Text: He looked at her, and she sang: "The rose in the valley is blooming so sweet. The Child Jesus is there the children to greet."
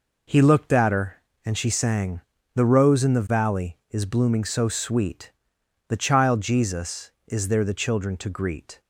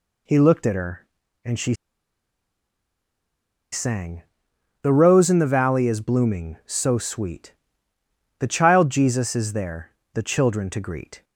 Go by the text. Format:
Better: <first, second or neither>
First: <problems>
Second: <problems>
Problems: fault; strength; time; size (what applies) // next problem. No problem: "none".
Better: first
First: none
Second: pauses between "she" and "sang"; strong; at 1.7 s; 1.9 s long // pauses between "there" and "the"; slight; at 9.8 s; 0.24 s long